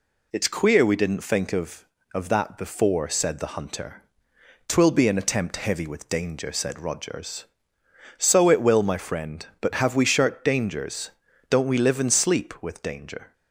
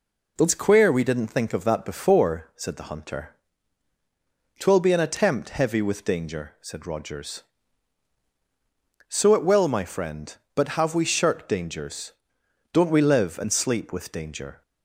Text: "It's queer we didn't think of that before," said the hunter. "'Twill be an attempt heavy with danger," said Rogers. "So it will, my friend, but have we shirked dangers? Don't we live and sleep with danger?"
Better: second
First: says "of" twice; at 2.1 s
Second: none

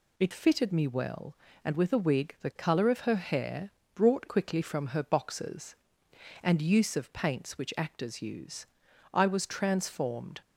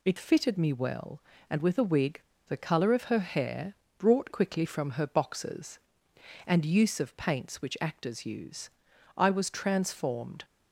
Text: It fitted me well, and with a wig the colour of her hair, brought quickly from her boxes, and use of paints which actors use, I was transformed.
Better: first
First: none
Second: pauses between "wig" and "the"; slight; at 2.2 s; 0.25 s long

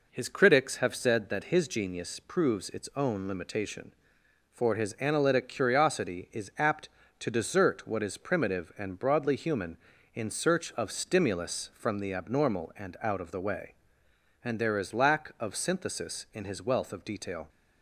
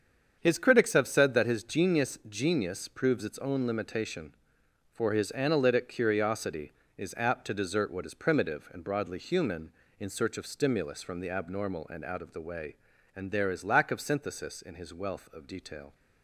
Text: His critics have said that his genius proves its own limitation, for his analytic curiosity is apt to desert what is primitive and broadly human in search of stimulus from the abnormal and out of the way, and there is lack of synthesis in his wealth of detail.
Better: first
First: none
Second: starts louder than the rest; strong; until 1.4 s; 7.5 dB // says "genius" twice; at 2.2 s

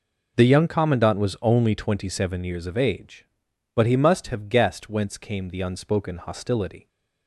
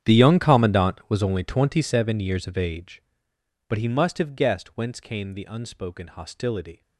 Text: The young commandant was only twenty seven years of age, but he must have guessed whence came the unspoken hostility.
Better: first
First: none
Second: gets quieter; strong; throughout; 19 dB

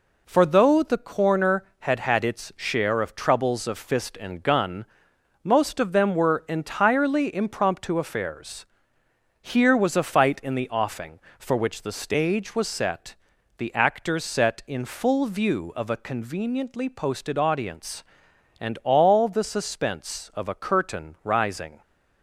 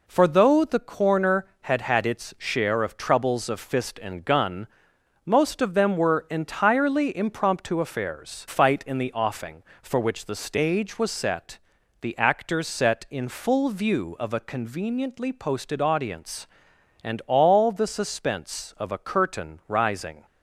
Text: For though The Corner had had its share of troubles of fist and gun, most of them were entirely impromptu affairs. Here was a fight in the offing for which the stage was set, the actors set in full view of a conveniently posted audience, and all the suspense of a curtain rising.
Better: first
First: none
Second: skips "Here was a"; at 8.4 s

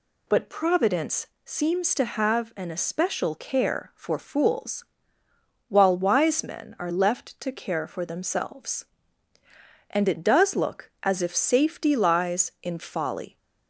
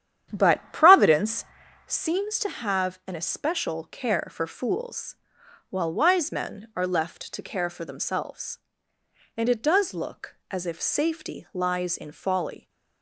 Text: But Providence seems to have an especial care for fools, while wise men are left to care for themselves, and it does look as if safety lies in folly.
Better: first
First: pauses between "Providence" and "seems"; slight; at 1.2 s; 0.18 s long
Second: starts louder than the rest; strong; until 2.0 s; 10 dB // pauses between "Providence" and "seems"; at 1.4 s; 0.44 s long

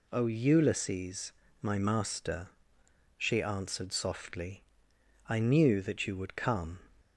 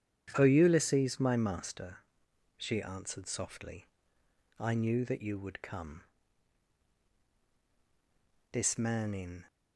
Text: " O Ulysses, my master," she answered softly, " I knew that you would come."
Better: first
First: none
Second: starts louder than the rest; strong; until 1.3 s; 9.5 dB // goes on to say "This man in"; noticeable; from 8.5 s on; 0.96 s long

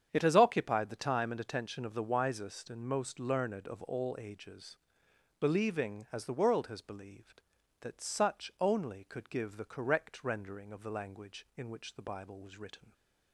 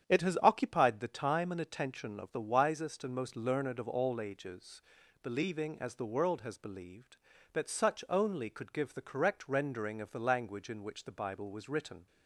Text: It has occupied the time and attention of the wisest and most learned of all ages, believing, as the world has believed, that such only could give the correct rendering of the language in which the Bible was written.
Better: neither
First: starts louder than the rest; strong; until 1.1 s; 8 dB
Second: starts louder than the rest; strong; until 1.1 s; 9 dB

